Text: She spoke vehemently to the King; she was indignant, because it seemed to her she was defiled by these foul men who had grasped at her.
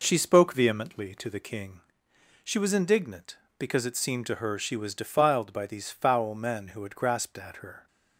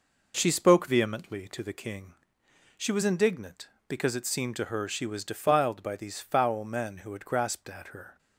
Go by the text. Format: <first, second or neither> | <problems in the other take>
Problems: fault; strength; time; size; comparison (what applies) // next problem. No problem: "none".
neither | none